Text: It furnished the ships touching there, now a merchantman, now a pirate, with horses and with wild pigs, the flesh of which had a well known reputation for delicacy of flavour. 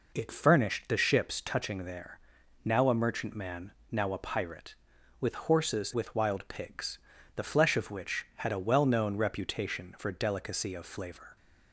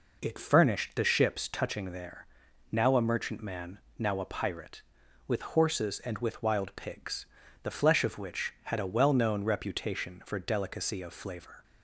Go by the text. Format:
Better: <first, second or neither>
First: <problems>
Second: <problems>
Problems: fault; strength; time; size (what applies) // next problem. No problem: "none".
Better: second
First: skips "and"; at 5.9 s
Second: none